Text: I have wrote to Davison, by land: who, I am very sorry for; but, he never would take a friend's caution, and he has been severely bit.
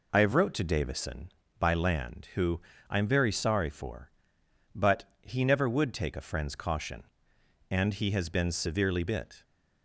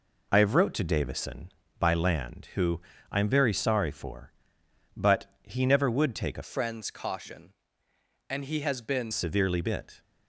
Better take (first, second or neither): first